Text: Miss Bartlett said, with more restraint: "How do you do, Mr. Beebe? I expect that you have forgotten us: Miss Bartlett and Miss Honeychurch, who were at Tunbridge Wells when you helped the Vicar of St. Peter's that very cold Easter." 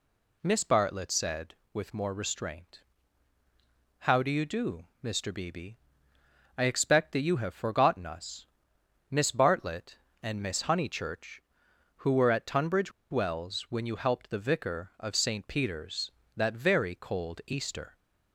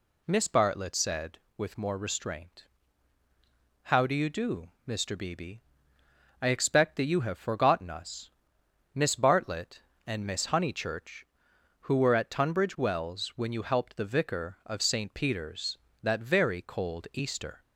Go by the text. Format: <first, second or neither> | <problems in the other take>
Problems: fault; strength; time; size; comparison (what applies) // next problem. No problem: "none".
second | pauses between "Tunbridge" and "Wells"; slight; at 12.8 s; 0.21 s long